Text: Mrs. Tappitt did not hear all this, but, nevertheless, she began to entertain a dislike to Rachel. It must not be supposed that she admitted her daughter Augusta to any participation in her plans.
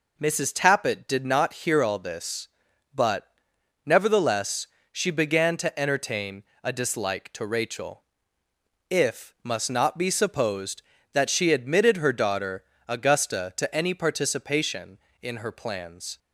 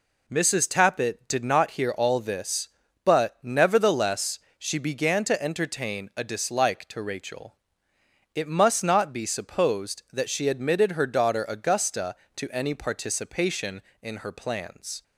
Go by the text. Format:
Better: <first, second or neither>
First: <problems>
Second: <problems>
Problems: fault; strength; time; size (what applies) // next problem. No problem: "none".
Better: second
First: pauses between "entertain" and "a"; slight; at 6.4 s; 0.18 s long // says "If" for "It"; at 8.8 s // pauses between "daughter" and "Augusta"; slight; at 12.6 s; 0.24 s long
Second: none